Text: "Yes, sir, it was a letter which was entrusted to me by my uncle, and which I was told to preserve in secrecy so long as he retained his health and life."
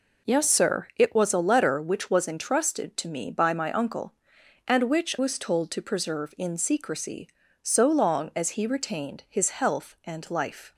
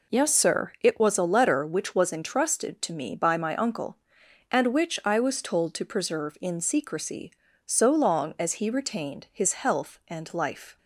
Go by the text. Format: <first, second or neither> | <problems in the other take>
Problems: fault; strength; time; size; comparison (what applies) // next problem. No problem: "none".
second | skips "I"; at 5.1 s